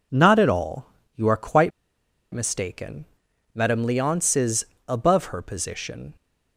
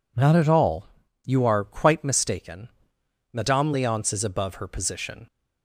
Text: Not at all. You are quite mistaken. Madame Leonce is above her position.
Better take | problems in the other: second | pauses between "quite" and "mistaken"; noticeable; at 1.7 s; 0.63 s long // pauses between "is" and "above"; slight; at 4.6 s; 0.20 s long

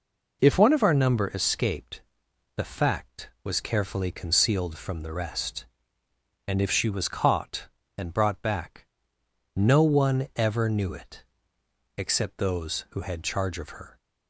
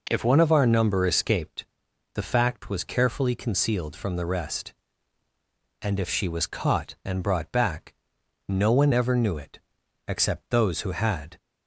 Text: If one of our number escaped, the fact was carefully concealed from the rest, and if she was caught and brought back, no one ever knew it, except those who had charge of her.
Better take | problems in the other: first | stops before "charge of her"; at 11.3 s

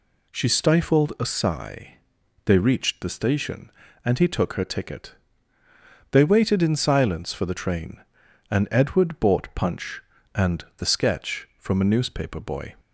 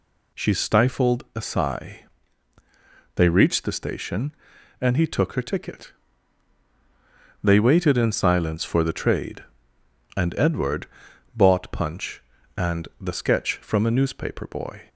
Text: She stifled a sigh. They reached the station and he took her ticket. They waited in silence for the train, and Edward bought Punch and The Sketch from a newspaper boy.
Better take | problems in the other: first | says "trade" for "train"; at 8.9 s // pauses between "Edward" and "bought"; noticeable; at 10.8 s; 0.50 s long

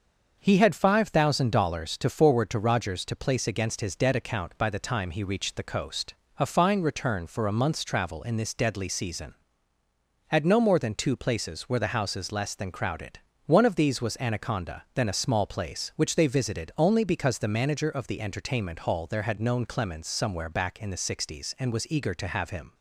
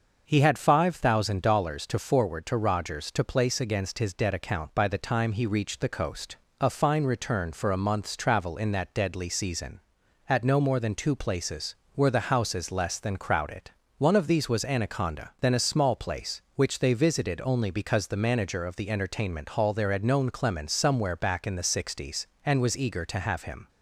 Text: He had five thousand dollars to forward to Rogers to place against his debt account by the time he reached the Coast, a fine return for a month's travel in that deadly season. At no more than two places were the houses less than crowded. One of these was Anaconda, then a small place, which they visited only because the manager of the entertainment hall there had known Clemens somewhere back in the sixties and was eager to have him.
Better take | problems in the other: second | starts louder than the rest; until 1.4 s; 6.5 dB; noticeable in the second // says "this" for "that"; at 8.3 s

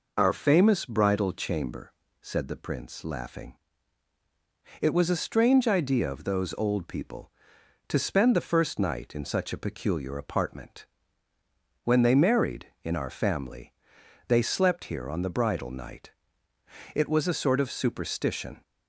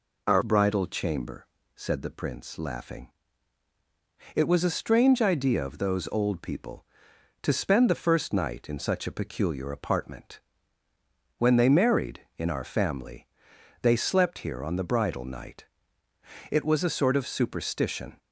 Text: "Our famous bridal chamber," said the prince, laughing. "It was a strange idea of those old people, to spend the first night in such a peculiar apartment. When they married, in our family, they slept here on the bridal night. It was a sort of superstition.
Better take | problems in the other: first | skips "famous"; at 0.4 s

